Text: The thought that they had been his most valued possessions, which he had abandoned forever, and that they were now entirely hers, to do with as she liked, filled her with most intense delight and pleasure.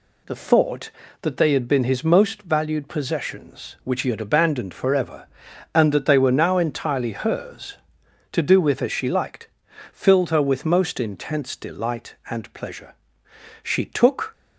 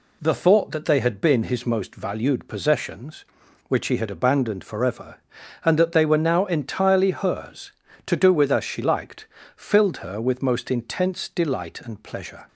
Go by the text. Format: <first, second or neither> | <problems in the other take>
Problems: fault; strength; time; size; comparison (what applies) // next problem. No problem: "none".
second | goes on to say "She took"; noticeable; from 13.6 s on; 0.70 s long